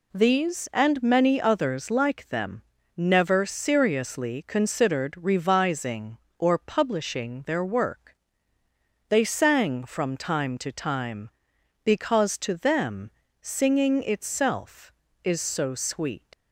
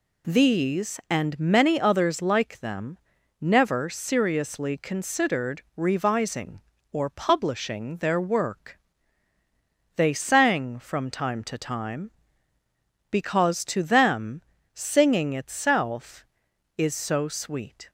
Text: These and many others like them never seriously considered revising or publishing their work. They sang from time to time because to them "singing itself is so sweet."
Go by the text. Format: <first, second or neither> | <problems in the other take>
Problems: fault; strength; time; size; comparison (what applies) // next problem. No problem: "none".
second | pauses between "them" and "never"; slight; at 2.6 s; 0.34 s long; also in the second // pauses between "them" and "singing"; slight; at 13.1 s; 0.30 s long; slight in the second // leaves "sweet" unfinished; at 16.3 s; 90 ms